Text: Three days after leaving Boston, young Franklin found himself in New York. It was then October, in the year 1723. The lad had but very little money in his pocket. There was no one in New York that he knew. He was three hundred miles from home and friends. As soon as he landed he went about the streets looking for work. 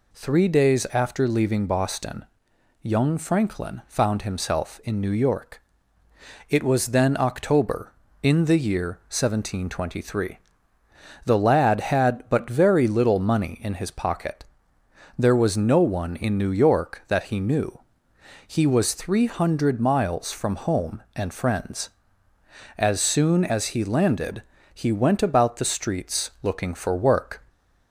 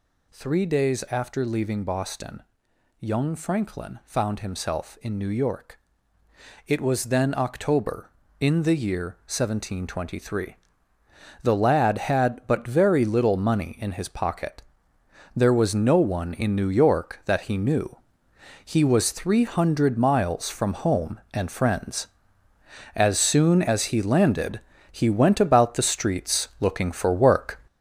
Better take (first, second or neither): first